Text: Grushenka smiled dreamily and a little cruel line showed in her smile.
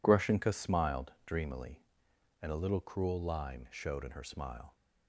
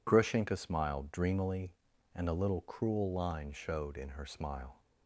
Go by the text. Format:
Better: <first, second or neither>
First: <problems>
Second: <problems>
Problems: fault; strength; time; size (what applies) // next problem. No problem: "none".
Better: neither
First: none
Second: none